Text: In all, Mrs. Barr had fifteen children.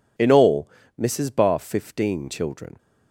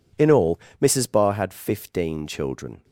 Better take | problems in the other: second | skips "had"; at 1.5 s

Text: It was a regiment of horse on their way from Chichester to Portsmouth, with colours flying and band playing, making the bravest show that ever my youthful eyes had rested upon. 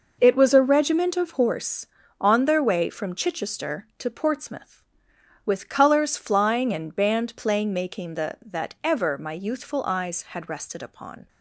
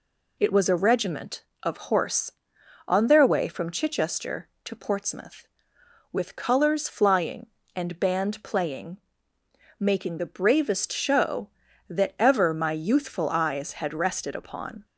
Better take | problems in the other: second | skips "bravest show"; at 8.3 s

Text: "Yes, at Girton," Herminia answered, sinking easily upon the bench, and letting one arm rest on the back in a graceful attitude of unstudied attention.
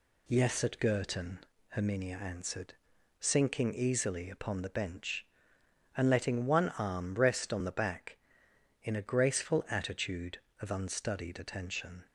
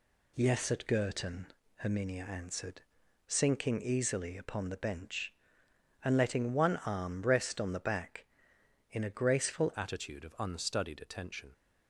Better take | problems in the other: first | changes voice at "attitude"; from 9.7 s on; 1.8 s long

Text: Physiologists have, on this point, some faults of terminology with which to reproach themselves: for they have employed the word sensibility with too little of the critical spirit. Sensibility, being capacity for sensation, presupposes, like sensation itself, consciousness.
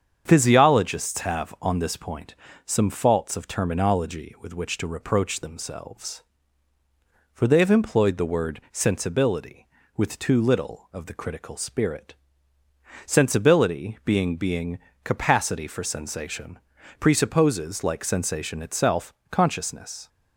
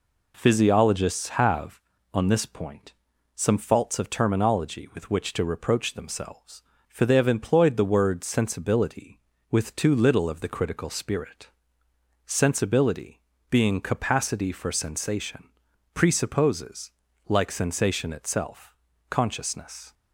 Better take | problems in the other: second | starts louder than the rest; strong; until 1.2 s; 7.5 dB // says "being" twice; at 14.3 s

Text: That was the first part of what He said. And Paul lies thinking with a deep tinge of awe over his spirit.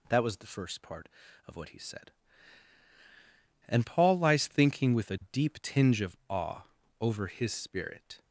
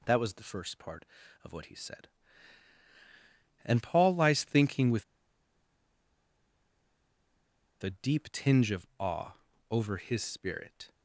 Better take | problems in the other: first | pauses between "with" and "a"; strong; at 5.0 s; 2.7 s long // pauses between "awe" and "over"; slight; at 9.3 s; 0.36 s long; slight in the first

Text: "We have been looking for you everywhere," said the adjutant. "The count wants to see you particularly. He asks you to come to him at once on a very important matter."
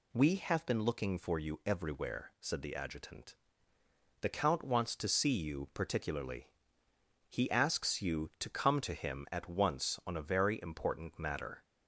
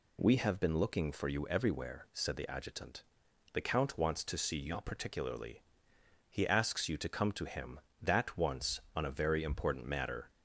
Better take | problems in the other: first | says "that" for "at"; at 8.0 s

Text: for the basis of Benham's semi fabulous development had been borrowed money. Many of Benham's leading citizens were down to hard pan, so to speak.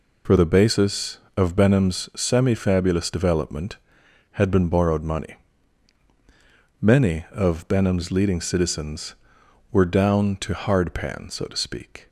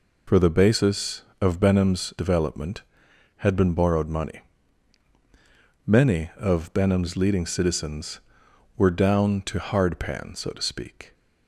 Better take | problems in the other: first | skips "semi fabulous"; at 2.1 s

